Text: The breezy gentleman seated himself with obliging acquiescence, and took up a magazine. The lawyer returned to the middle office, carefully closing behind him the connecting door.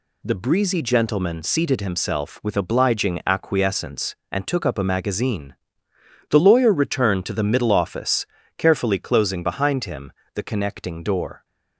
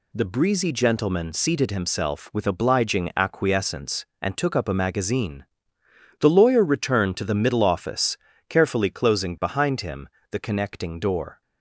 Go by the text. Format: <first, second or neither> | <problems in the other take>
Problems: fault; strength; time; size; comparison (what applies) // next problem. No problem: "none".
neither | pauses between "him" and "the"; slight; the same in both